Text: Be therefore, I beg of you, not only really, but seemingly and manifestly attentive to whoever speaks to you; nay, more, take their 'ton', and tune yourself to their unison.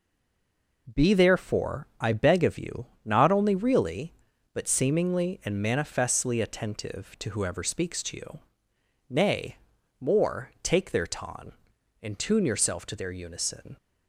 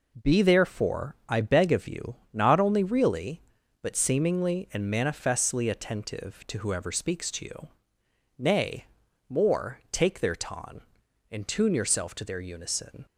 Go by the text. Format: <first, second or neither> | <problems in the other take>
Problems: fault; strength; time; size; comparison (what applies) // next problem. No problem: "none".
second | stays silent before the first word; slight; until 0.8 s; 0.8 s long